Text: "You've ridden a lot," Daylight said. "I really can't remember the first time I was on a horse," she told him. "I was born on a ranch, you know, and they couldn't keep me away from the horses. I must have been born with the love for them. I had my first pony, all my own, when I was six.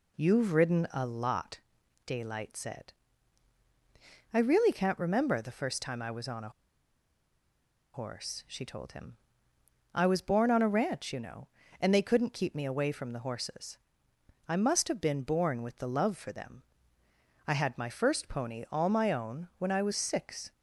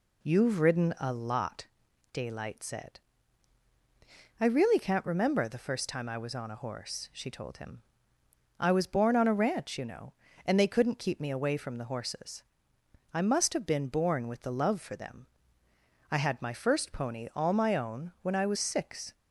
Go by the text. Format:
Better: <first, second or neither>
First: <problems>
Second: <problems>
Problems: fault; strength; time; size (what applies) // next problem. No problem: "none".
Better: second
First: pauses between "a" and "horse"; strong; at 6.5 s; 1.4 s long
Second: none